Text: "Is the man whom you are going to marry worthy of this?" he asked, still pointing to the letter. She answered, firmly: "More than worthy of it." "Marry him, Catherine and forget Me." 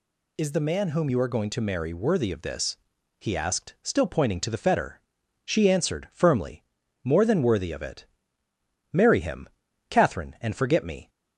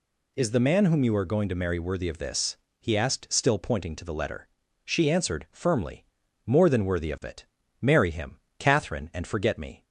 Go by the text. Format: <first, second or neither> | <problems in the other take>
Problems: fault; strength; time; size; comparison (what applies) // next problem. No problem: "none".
second | says "fetter" for "letter"; at 4.5 s